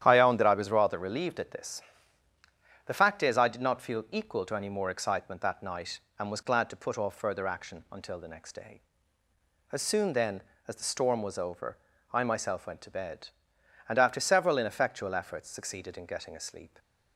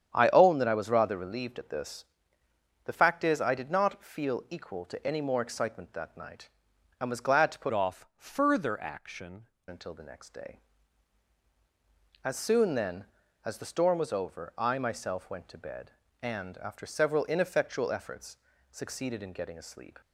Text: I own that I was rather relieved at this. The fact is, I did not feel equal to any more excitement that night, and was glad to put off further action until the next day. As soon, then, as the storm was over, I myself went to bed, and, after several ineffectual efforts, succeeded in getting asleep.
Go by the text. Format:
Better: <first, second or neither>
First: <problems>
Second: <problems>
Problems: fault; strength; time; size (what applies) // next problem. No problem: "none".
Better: first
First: starts louder than the rest; strong; until 1.0 s; 10 dB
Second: starts louder than the rest; strong; until 1.1 s; 8.5 dB // changes voice from "off" to "action"; from 7.7 to 9.4 s; 1.7 s long